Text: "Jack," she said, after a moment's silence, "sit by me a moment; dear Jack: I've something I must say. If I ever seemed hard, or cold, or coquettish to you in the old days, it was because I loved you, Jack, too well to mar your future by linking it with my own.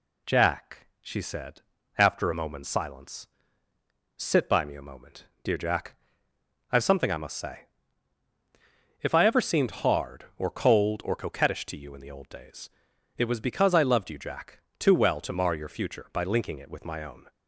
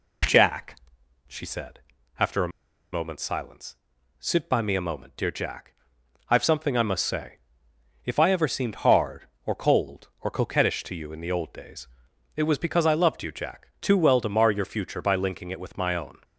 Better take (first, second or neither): first